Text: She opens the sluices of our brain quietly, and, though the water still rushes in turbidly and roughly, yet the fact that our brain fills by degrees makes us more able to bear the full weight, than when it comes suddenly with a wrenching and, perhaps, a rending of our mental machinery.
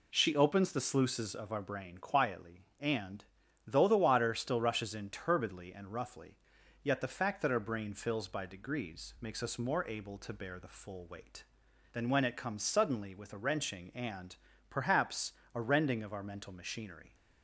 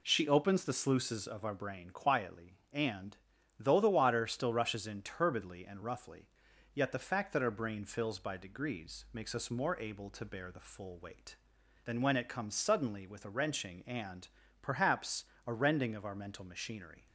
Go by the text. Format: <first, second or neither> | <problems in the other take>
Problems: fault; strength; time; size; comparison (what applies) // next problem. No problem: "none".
neither | none